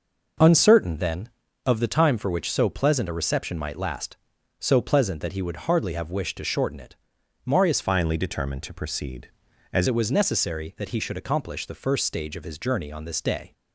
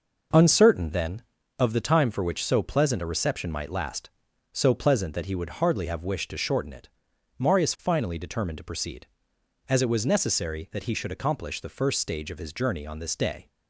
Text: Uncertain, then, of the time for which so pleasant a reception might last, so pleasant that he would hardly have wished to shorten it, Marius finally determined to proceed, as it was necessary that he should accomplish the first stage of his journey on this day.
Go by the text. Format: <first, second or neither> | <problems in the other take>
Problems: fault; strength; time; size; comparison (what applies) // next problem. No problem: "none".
second | changes voice from "finally" to "as"; from 7.8 to 9.8 s; 2.0 s long